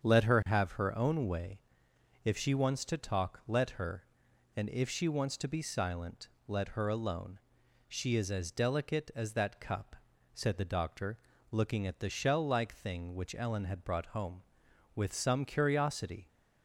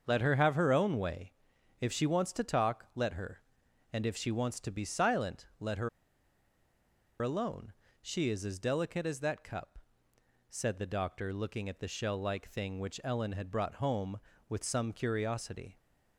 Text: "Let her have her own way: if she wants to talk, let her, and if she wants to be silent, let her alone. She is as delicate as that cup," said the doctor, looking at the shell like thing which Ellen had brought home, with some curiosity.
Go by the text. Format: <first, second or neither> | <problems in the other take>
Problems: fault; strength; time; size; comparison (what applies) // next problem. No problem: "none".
first | starts louder than the rest; until 1.0 s; 6.5 dB; strong in the first // pauses between "her" and "alone"; strong; at 5.8 s; 1.3 s long